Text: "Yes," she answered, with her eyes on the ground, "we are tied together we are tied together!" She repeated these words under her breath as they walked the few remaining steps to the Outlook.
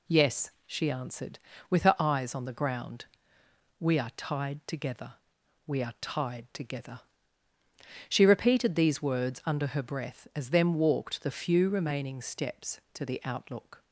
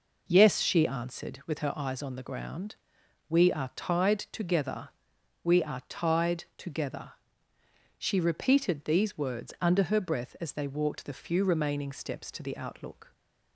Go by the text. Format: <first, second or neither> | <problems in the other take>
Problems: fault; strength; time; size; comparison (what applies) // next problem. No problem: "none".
second | pauses between "together" and "we"; noticeable; at 5.1 s; 0.52 s long; noticeable in the second // says "them" for "they"; at 10.5 s